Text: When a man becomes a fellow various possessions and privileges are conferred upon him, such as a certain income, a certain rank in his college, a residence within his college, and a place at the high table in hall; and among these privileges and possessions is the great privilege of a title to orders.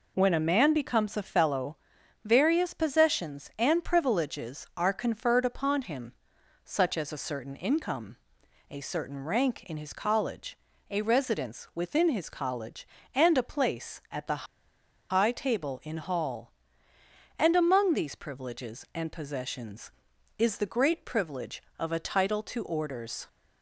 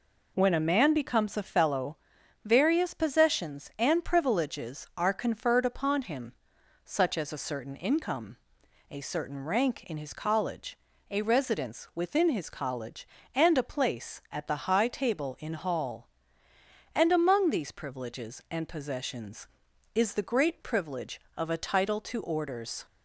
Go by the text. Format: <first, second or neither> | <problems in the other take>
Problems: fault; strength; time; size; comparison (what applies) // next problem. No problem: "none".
second | pauses between "fellow" and "various"; noticeable; at 1.7 s; 0.48 s long; noticeable in the second // pauses between "the" and "high"; noticeable; at 14.4 s; 0.65 s long